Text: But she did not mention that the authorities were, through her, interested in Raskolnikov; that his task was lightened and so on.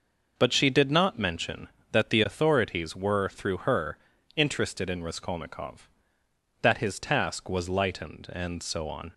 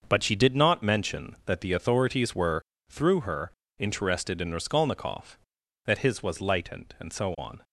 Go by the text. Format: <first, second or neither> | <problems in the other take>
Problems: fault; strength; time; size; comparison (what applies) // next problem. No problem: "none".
first | starts louder than the rest; until 1.0 s; 6.5 dB // skips "task"; at 6.2 s